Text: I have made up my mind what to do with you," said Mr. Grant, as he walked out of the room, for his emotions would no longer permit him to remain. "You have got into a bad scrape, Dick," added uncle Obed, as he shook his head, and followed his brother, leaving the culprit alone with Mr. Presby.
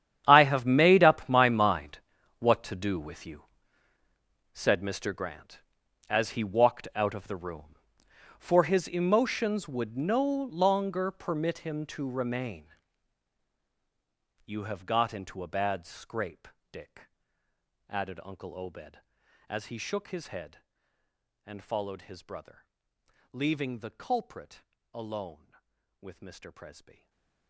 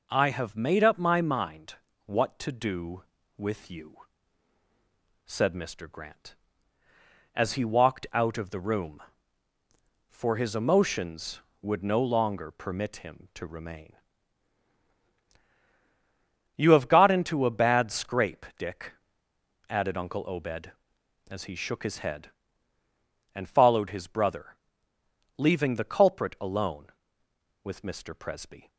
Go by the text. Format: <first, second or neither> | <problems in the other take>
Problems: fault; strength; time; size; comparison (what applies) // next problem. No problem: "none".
second | gets quieter; strong; throughout; 19 dB // pauses between "mind" and "what"; at 1.9 s; 0.40 s long; slight in the second // pauses between "culprit" and "alone"; slight; at 24.6 s; 0.28 s long // stays silent after the last word; slight; from 26.9 s on; 0.5 s long